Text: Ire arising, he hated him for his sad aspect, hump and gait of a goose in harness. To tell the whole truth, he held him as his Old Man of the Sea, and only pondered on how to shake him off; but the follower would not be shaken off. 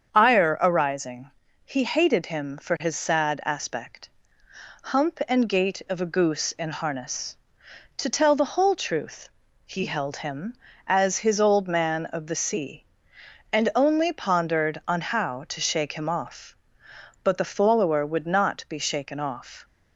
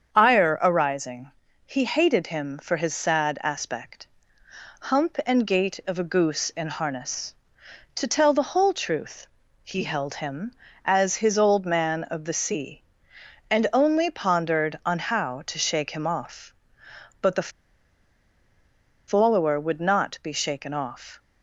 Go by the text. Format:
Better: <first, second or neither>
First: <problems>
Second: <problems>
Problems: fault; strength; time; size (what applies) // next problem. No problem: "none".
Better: first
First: starts louder than the rest; strong; until 1.1 s; 7 dB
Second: starts louder than the rest; strong; until 1.1 s; 7 dB // pauses between "the" and "follower"; strong; at 17.4 s; 1.5 s long